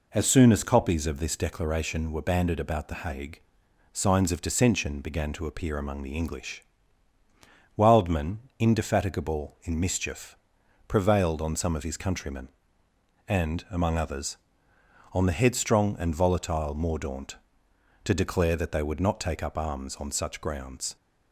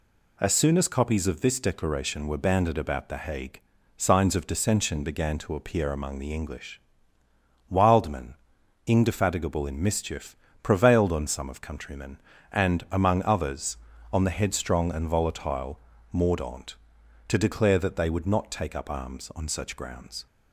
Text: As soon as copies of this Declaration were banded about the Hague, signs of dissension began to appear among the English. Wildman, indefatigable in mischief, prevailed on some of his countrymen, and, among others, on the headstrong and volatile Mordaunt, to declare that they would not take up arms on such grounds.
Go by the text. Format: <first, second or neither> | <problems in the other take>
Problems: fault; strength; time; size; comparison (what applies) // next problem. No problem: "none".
first | skips "his"; at 11.6 s // pauses between "volatile" and "Mordaunt"; slight; at 15.8 s; 0.32 s long